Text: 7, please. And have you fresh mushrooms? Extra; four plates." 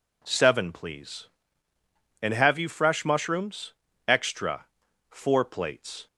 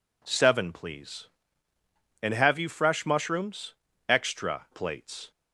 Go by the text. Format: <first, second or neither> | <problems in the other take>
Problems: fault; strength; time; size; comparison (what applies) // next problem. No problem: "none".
first | skips "four"; at 4.6 s